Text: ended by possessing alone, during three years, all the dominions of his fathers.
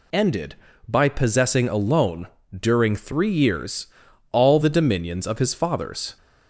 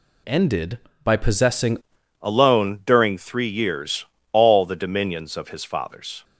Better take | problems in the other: first | changes voice at "alone"; from 2.2 s on; 4.0 s long

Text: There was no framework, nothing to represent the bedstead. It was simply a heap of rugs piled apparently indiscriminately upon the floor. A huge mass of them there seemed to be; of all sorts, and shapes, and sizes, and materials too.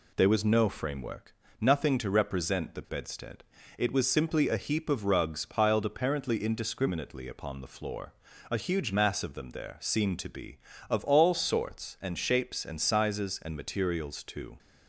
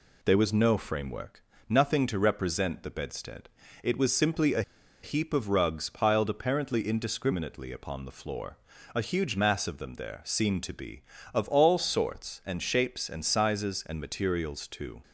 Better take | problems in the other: first | pauses between "a" and "heap"; at 4.6 s; 0.41 s long

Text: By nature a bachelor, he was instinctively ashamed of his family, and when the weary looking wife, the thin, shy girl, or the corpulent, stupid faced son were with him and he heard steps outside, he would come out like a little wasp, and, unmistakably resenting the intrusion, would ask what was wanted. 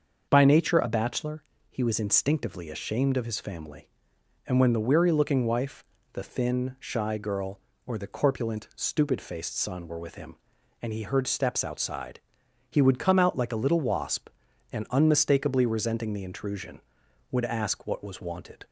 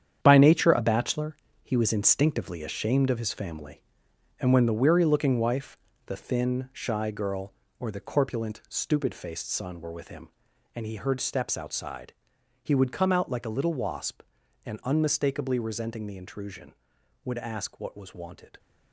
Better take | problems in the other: first | gets quieter; strong; throughout; 9 dB // starts louder than the rest; strong; until 1.2 s; 9 dB; also in the first

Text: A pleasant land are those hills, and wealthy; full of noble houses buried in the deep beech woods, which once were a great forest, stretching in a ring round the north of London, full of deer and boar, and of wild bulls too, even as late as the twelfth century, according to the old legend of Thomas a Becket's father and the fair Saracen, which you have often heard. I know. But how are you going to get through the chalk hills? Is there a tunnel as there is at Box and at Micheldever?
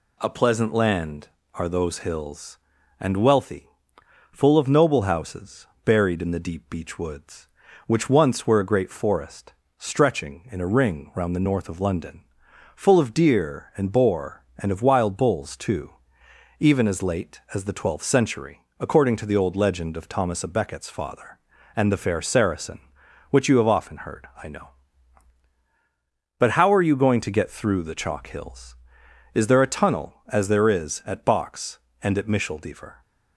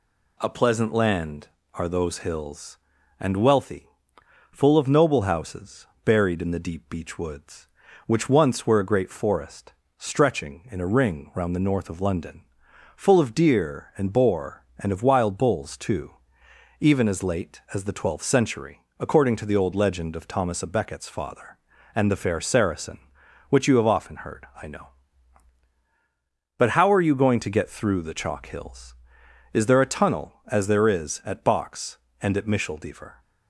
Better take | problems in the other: neither | pauses between "houses" and "buried"; slight; the same in both

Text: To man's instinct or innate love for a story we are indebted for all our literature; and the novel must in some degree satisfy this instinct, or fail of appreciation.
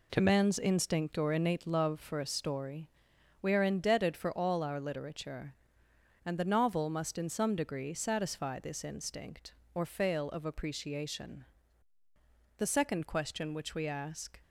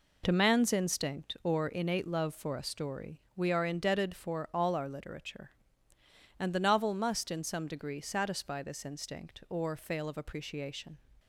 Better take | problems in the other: second | pauses between "story" and "we"; noticeable; at 2.8 s; 0.52 s long; slight in the second // goes on to say "The second question which we ask"; strong; from 12.5 s on; 1.8 s long

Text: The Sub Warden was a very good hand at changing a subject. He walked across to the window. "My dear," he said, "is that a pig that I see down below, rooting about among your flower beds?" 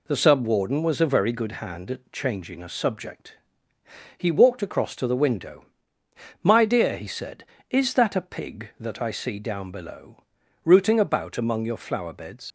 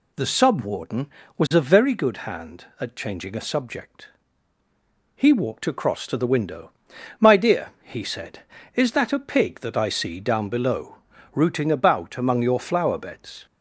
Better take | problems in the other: second | leaves "beds" unfinished; at 12.4 s; 120 ms

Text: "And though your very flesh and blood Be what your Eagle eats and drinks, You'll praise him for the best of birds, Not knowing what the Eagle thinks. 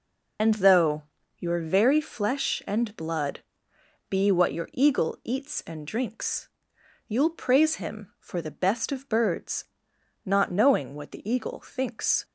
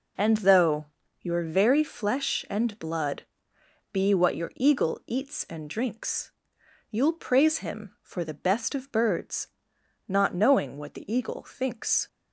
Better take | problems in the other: second | loses the start of "And"; at 0.3 s; 55 ms // pauses between "though" and "your"; slight; at 1.0 s; 0.36 s long; slight in the second // pauses between "blood" and "Be"; noticeable; at 3.4 s; 0.66 s long; noticeable in the second

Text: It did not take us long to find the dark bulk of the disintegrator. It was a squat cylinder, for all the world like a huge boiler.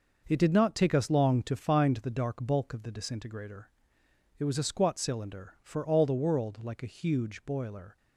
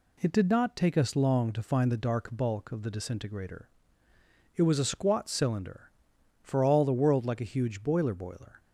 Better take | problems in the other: first | says "boiler" twice; at 8.1 s

